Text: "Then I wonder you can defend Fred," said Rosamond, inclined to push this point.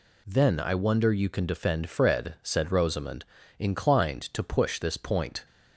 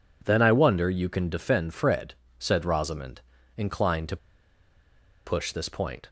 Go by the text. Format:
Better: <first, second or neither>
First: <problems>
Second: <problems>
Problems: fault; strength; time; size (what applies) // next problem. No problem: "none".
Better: first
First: none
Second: pauses between "to" and "push"; at 4.1 s; 1.0 s long